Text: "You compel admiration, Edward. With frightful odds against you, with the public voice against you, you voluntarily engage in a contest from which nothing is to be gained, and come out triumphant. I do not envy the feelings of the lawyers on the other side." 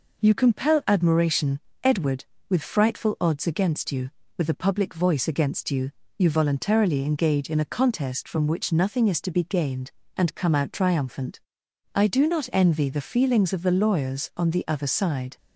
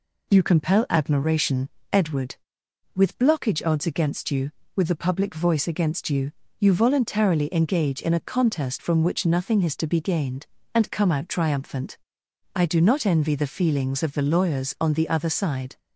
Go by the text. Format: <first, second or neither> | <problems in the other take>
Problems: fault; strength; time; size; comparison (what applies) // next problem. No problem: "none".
first | says "blockage" for "frightful"; at 3.1 s